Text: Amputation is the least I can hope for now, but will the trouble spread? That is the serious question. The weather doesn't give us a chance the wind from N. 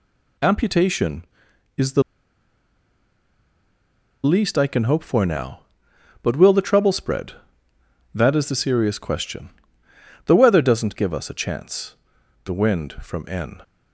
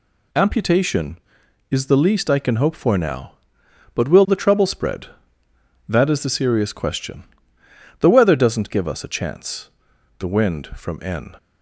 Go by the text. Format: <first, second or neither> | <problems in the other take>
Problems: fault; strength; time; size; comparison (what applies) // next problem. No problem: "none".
second | pauses between "the" and "least"; strong; at 2.0 s; 2.2 s long // pauses between "chance" and "the"; noticeable; at 11.9 s; 0.48 s long; noticeable in the second